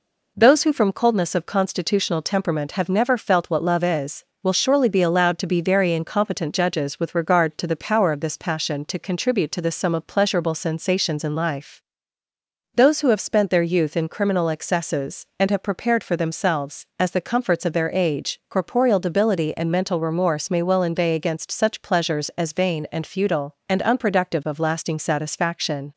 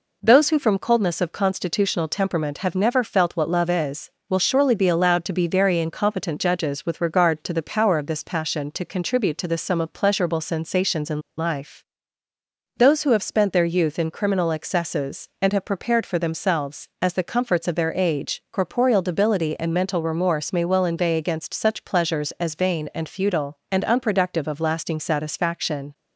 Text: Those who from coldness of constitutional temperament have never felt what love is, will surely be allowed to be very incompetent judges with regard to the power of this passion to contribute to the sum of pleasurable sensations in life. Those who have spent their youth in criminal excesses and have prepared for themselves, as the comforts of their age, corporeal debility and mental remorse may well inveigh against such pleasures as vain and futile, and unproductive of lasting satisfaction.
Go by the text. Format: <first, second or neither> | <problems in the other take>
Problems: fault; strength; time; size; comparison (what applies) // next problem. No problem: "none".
first | pauses between "in" and "life"; slight; at 11.2 s; 0.16 s long